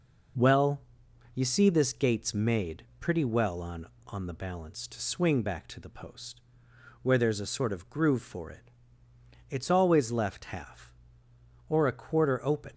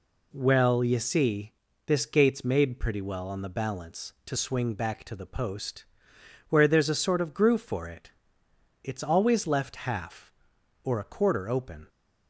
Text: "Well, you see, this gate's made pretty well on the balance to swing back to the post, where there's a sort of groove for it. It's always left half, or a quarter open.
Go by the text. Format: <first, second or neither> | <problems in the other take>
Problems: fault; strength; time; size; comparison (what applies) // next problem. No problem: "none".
second | pauses between "made" and "pretty"; slight; at 2.8 s; 0.16 s long // says "on" twice; at 4.0 s